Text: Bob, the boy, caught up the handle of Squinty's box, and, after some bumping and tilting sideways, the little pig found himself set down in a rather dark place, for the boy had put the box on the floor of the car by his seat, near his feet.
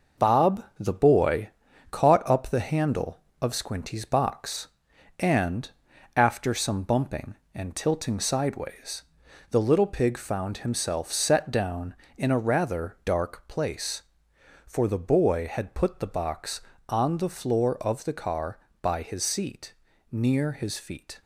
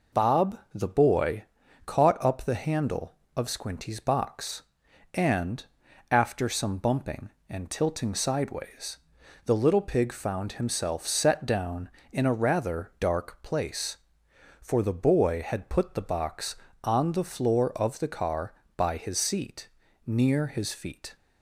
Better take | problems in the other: second | gets quieter; noticeable; throughout; 5 dB

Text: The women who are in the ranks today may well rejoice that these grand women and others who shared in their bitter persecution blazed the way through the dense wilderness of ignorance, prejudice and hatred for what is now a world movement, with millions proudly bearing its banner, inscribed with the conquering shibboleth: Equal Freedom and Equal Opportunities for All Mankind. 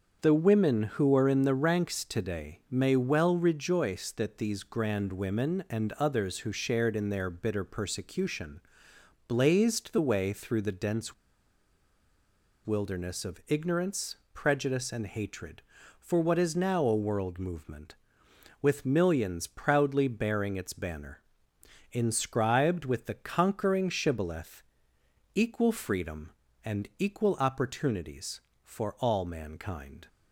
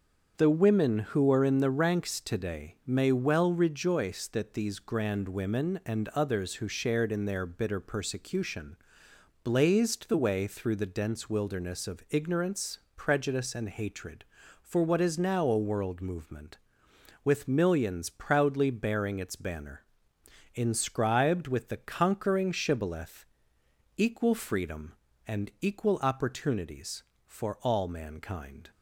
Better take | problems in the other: second | starts louder than the rest; until 1.2 s; 6.5 dB; also in the second // pauses between "persecution" and "blazed"; noticeable; at 8.5 s; 0.70 s long; noticeable in the second // pauses between "dense" and "wilderness"; strong; at 11.1 s; 1.5 s long

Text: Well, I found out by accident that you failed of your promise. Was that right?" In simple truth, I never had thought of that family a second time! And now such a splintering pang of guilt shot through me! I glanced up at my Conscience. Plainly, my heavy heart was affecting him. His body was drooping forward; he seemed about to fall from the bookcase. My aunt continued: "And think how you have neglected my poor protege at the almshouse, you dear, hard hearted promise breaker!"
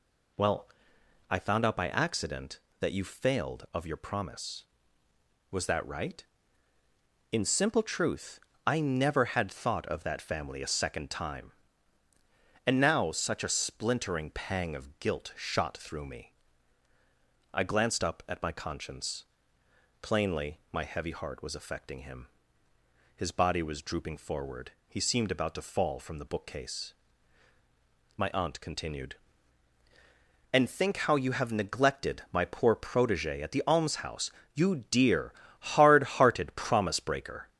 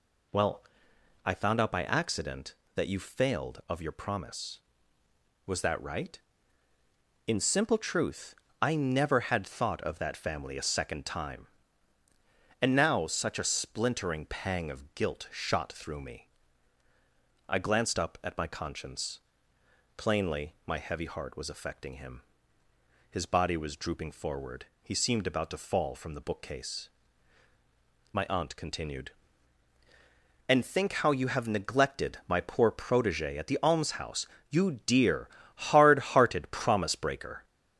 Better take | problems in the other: neither | none

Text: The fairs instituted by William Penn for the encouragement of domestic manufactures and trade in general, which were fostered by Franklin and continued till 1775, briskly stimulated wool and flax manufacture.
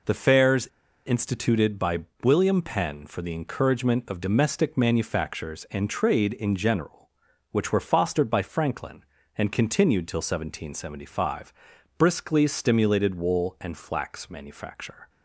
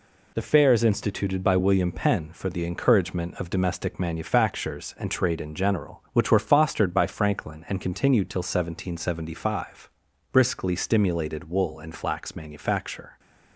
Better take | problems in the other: second | pauses between "fairs" and "instituted"; at 0.6 s; 0.39 s long // pauses between "by" and "William"; slight; at 2.0 s; 0.18 s long

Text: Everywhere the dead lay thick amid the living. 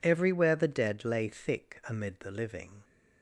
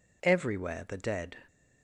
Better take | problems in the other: first | stops before "lay thick amid the living"; at 1.4 s

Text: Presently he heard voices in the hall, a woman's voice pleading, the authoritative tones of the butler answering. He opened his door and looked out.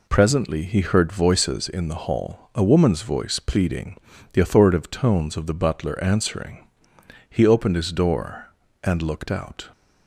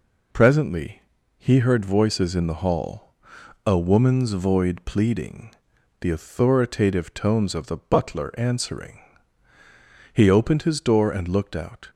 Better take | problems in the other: first | pauses between "Presently" and "he"; slight; at 1.0 s; 0.36 s long // says "void" for "voice"; at 4.3 s

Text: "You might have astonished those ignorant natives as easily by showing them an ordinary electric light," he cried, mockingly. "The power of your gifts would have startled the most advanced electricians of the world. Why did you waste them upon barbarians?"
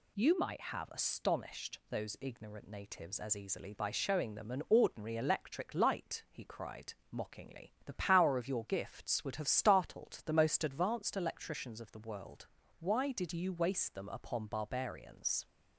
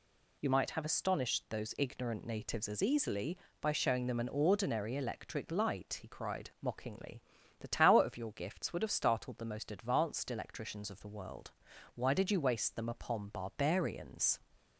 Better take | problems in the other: first | says "tower" for "power"; at 7.6 s

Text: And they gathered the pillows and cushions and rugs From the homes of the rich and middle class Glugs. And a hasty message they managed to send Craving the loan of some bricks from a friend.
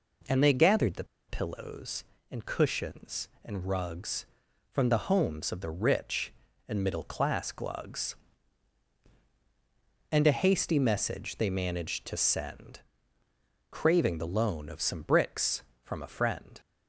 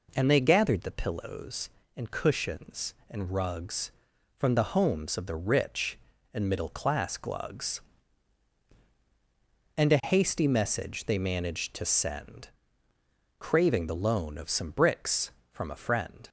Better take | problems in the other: second | pauses between "the" and "pillows"; slight; at 1.0 s; 0.24 s long // pauses between "send" and "Craving"; noticeable; at 12.7 s; 0.90 s long; noticeable in the second

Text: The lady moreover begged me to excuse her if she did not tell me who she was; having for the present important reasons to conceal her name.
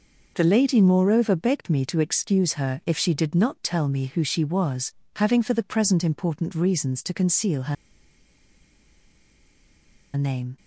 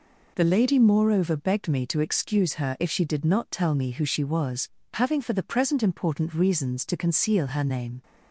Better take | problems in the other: second | pauses between "her" and "name"; strong; at 7.7 s; 2.4 s long

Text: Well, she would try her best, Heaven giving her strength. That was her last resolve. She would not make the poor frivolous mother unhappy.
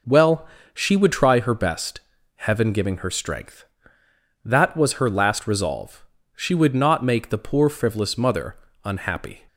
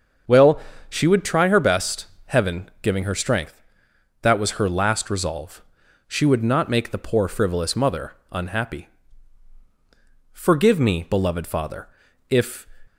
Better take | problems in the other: first | starts louder than the rest; until 1.5 s; 7 dB // pauses between "mother" and "unhappy"; slight; at 8.1 s; 0.18 s long; slight in the first // goes on to say "Forgive me beloved father if"; strong; from 10.3 s on; 2.3 s long

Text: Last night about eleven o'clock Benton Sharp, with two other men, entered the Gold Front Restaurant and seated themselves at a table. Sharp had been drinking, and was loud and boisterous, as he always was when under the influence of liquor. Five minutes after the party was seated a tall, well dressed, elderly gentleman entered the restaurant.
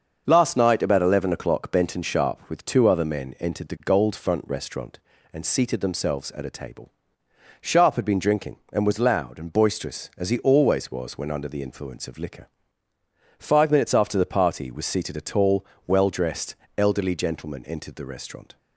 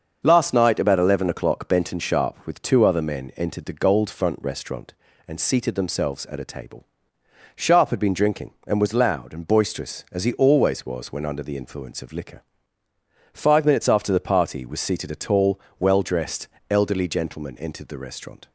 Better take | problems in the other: neither | starts louder than the rest; the same in both

